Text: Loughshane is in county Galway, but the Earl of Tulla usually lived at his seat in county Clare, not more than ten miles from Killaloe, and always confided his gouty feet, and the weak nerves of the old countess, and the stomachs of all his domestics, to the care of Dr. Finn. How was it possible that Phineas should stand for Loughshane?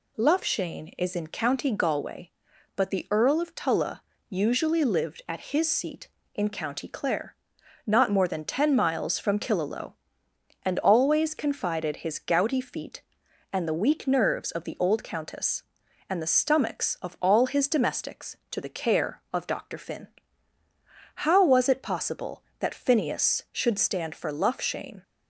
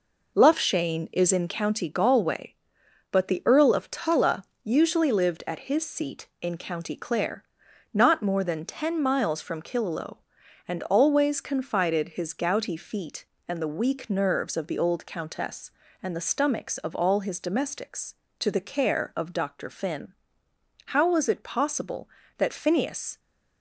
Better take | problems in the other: first | pauses between "Tulla" and "usually"; slight; at 4.4 s; 0.20 s long; slight in the first // stops before "should stand for Loughshane"; at 23.1 s

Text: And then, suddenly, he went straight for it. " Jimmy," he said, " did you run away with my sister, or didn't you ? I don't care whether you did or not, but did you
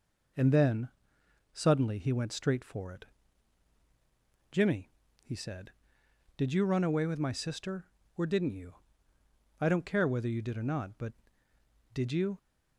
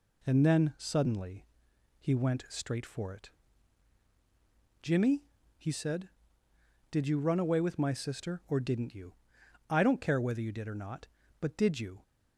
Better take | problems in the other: neither | none

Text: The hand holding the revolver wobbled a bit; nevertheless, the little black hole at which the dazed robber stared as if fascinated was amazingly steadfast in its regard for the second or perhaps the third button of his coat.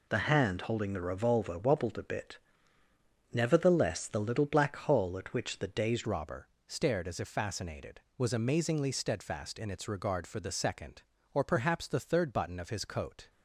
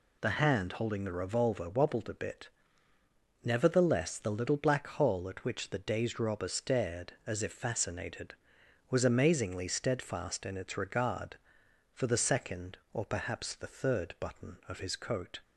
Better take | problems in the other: second | changes voice at "robber"; from 6.0 s on; 7.2 s long // pauses between "robber" and "stared"; slight; at 6.4 s; 0.20 s long

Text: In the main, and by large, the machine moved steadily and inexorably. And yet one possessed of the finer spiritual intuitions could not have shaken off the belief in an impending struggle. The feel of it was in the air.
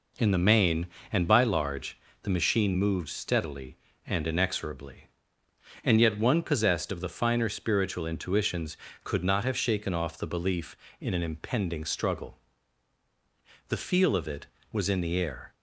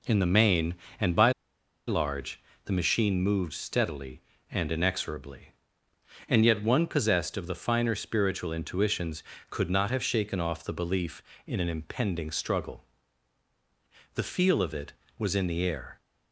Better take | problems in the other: first | pauses between "by" and "large"; noticeable; at 1.3 s; 0.56 s long

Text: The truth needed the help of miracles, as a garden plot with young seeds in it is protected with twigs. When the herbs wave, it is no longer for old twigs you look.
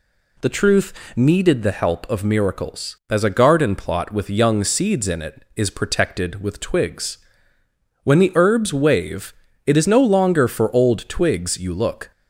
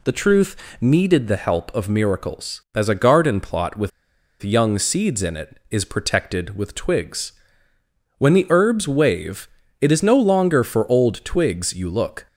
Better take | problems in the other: first | pauses between "truth" and "needed"; slight; at 0.5 s; 0.24 s long; slight in the first // pauses between "with" and "young"; noticeable; at 3.9 s; 0.52 s long

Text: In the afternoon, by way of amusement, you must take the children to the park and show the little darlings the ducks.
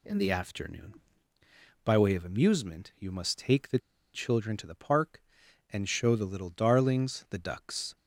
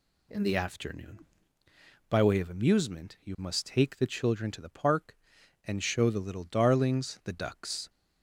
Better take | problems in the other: second | pauses between "the" and "children"; at 3.7 s; 0.36 s long

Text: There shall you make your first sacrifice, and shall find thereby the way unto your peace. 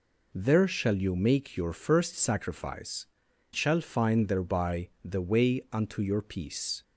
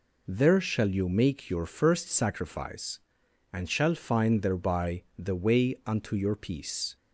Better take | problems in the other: second | skips "and"; at 3.3 s // pauses between "thereby" and "the"; slight; at 4.8 s; 0.16 s long; slight in the second

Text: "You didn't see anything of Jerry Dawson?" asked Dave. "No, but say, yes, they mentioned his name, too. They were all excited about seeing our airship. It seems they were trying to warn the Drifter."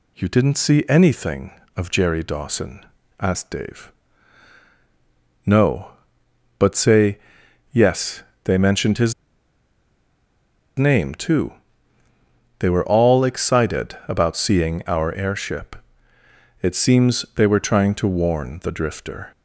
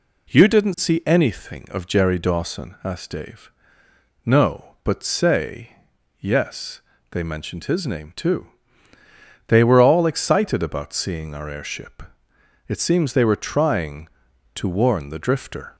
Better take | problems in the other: second | pauses between "his" and "name"; strong; at 9.1 s; 1.6 s long

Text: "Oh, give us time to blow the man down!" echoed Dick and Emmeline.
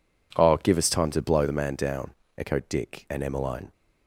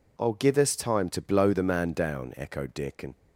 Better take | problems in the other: first | stops before "Emmeline"; at 3.1 s

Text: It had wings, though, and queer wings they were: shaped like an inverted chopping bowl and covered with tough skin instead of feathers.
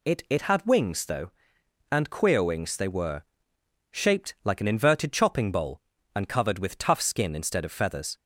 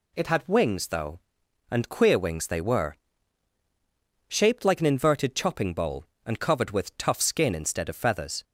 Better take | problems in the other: second | says "It" twice; at 0.2 s

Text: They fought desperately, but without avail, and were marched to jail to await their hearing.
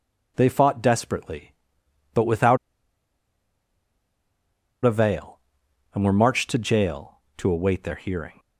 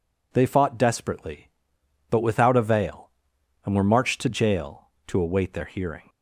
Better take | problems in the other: second | pauses between "without" and "avail"; strong; at 2.5 s; 2.2 s long

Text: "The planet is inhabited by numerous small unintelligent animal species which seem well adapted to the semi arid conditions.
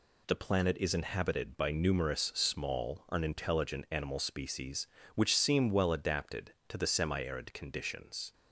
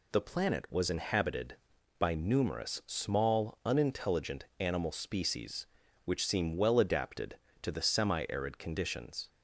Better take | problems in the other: first | says "was" for "is"; at 0.7 s

